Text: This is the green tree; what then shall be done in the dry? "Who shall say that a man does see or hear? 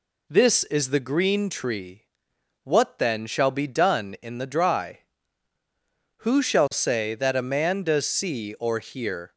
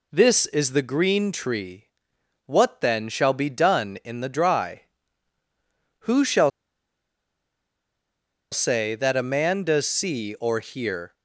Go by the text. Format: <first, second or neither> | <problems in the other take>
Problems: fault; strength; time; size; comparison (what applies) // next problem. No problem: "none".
first | pauses between "shall" and "say"; strong; at 6.4 s; 2.0 s long